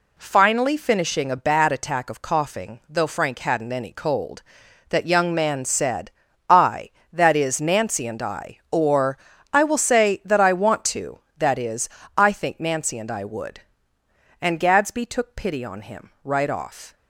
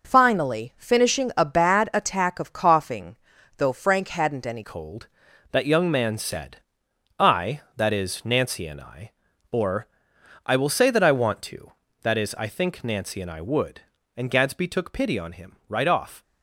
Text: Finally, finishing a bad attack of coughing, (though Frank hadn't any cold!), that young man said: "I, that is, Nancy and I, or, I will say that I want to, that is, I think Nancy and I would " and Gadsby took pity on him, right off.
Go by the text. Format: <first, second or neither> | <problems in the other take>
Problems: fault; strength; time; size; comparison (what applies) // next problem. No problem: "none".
first | changes voice at "cold"; from 4.6 s on; 11.6 s long